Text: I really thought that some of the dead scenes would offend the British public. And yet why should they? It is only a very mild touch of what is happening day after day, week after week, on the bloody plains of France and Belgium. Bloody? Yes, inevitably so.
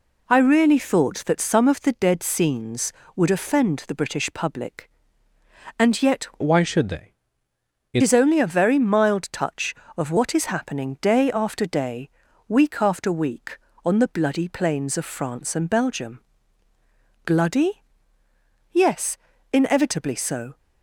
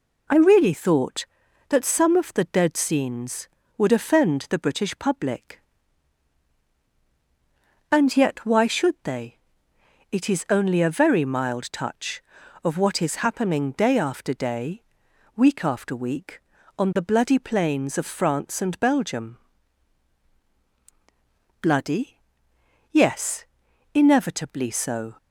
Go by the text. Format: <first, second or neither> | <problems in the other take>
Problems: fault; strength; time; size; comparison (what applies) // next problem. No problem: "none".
second | changes voice from "why" to "It"; from 6.4 to 8.0 s; 1.6 s long